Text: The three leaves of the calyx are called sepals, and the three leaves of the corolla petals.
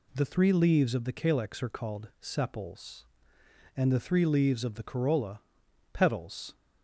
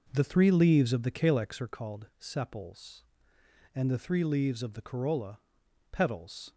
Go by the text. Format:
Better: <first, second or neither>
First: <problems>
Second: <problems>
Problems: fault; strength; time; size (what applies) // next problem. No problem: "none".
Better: first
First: pauses between "corolla" and "petals"; noticeable; at 5.4 s; 0.52 s long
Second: starts louder than the rest; noticeable; until 1.6 s; 5 dB // pauses between "corolla" and "petals"; noticeable; at 5.3 s; 0.52 s long